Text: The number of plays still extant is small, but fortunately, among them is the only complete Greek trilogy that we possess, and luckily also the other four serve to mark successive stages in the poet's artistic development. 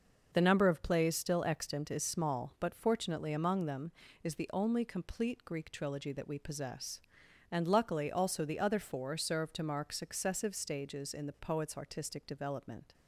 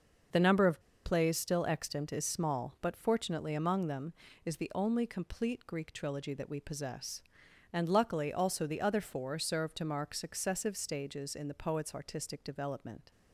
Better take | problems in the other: first | starts louder than the rest; noticeable; until 1.5 s; 6 dB; noticeable in the first // pauses between "of" and "plays"; slight; at 0.8 s; 0.23 s long

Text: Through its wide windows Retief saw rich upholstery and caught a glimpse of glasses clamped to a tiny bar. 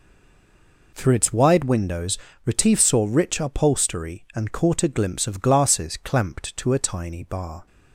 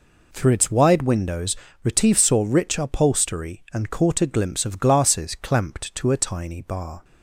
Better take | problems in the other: second | stays silent before the first word; slight; until 0.9 s; 0.9 s long // pauses between "windows" and "Retief"; slight; at 2.1 s; 0.28 s long; slight in the second

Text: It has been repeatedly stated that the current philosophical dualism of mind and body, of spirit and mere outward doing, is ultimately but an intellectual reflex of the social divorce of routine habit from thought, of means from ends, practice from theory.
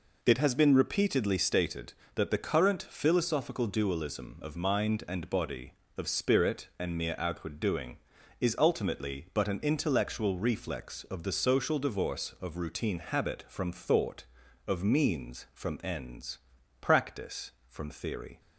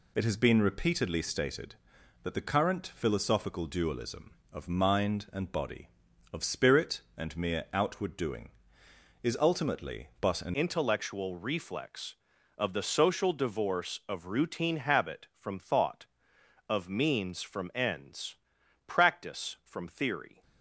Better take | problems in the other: first | changes voice at "intellectual"; from 10.5 s on; 9.9 s long

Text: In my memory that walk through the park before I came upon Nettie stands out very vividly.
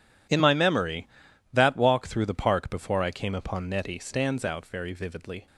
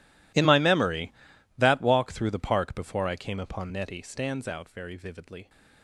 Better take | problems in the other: first | gets quieter; strong; throughout; 22.5 dB

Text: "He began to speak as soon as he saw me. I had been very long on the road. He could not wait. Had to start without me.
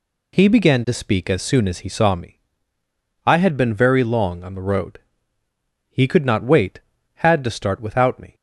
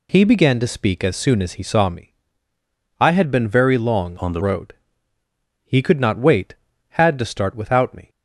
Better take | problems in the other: first | changes voice from "on" to "the"; from 4.1 to 4.4 s; 0.3 s long

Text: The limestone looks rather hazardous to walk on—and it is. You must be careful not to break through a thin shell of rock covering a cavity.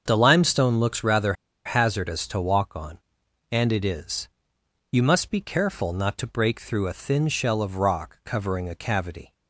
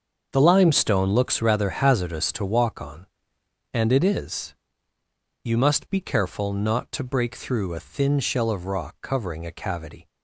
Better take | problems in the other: second | starts louder than the rest; until 1.0 s; 6.5 dB; also in the second // pauses between "rather" and "hazardous"; slight; at 1.3 s; 0.32 s long

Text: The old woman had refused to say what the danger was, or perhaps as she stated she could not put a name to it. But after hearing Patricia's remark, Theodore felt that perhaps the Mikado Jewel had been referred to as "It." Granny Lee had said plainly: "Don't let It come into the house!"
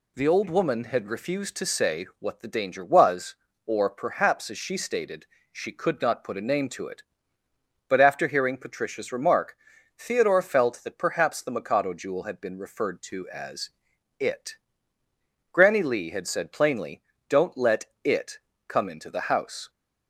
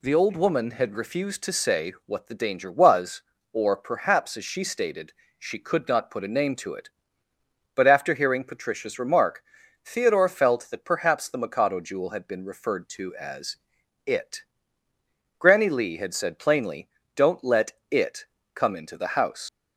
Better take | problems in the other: first | pauses between "stated" and "she"; slight; at 5.1 s; 0.26 s long; slight in the first // pauses between "as" and "It"; noticeable; at 13.5 s; 0.50 s long; noticeable in the first // pauses between "let" and "It"; slight; at 17.7 s; 0.18 s long; slight in the first // pauses between "It" and "come"; slight; at 18.2 s; 0.30 s long; slight in the first // leaves "house" unfinished; at 19.4 s; 80 ms

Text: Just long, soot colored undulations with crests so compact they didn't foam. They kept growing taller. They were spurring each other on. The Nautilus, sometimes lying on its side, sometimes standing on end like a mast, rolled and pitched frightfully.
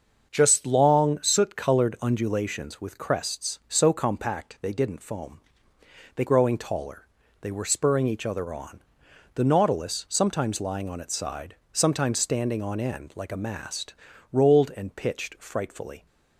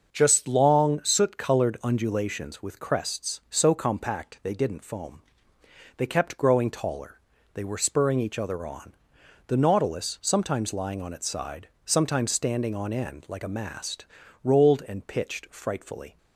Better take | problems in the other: second | starts louder than the rest; until 1.3 s; 6.5 dB; also in the second // skips "kept"; at 6.2 s

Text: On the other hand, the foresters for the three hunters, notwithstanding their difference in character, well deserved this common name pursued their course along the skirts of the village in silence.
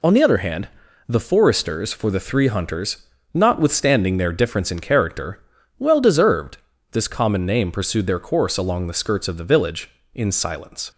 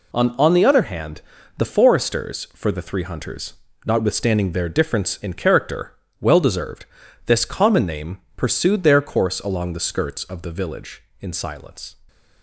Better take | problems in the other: first | says "On" twice; at 0.3 s // pauses between "deserved" and "this"; at 6.8 s; 0.40 s long; slight in the first // pauses between "name" and "pursued"; slight; at 8.2 s; 0.16 s long

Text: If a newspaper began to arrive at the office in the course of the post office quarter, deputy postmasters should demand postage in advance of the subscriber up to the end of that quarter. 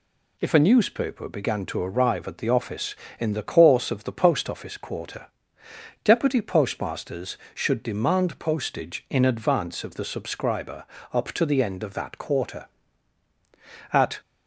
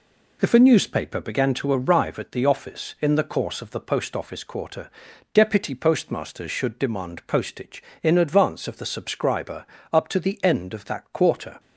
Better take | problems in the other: second | pauses between "subscriber" and "up"; slight; at 10.8 s; 0.26 s long; slight in the second // goes on to say "At"; slight; from 13.9 s on; 0.28 s long

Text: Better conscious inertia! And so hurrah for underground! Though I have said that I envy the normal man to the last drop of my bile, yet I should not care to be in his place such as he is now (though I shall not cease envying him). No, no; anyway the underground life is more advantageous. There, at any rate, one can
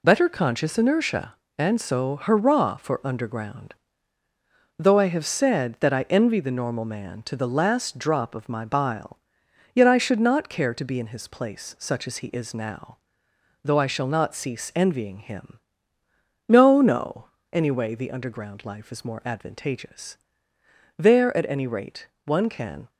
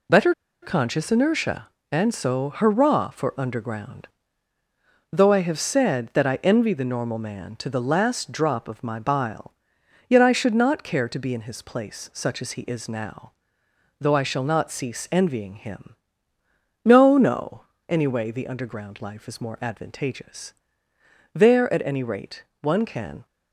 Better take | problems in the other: first | pauses between "Better" and "conscious"; slight; at 0.3 s; 0.28 s long

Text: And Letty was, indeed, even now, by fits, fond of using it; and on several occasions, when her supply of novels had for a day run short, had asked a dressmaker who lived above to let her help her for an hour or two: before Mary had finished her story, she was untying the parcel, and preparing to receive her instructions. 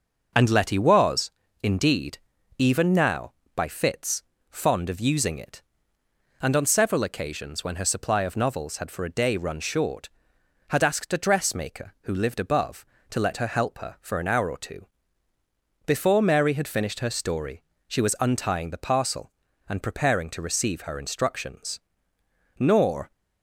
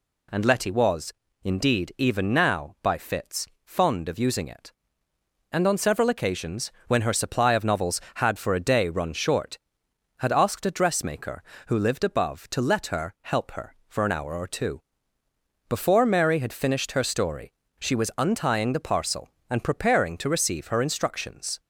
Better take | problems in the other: second | goes on to say "Nor"; from 22.5 s on; 0.52 s long

